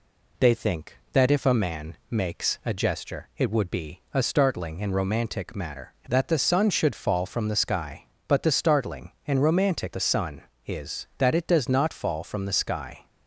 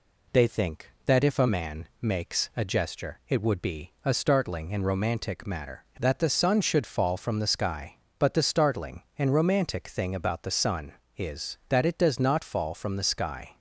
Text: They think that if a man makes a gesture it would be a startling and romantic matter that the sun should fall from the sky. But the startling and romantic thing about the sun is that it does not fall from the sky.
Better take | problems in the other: second | skips "thing about"; at 9.9 s

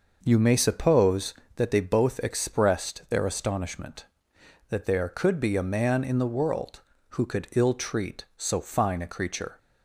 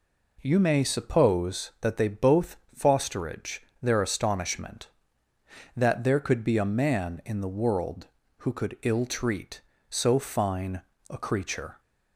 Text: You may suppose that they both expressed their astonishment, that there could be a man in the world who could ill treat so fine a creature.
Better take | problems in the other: first | says "fosterage" for "expressed"; at 2.7 s // pauses between "fine" and "a"; slight; at 10.7 s; 0.30 s long

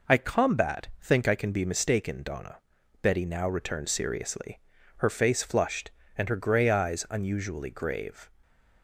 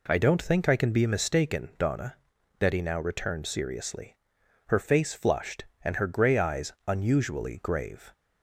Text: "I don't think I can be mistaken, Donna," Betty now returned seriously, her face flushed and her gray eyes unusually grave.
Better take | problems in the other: second | says "combat" for "don't"; at 0.1 s

